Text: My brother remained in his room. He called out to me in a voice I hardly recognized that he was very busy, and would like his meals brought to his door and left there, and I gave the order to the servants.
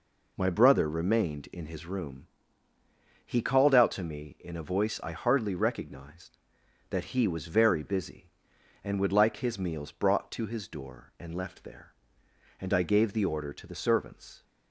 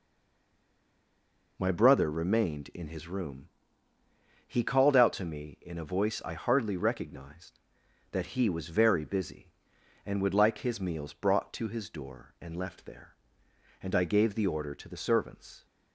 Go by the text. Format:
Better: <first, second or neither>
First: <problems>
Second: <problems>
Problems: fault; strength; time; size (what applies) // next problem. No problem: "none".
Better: first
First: none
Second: stays silent before the first word; noticeable; until 1.5 s; 1.5 s long